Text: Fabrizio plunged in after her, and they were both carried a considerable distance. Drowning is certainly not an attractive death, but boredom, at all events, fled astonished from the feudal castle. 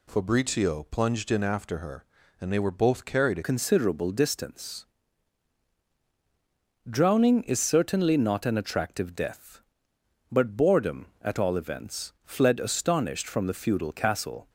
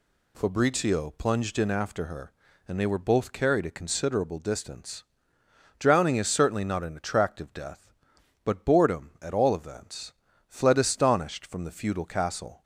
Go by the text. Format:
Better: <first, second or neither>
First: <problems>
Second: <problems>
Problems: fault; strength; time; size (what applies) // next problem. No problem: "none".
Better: second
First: changes voice at "considerable"; from 3.4 s on; 11.0 s long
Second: none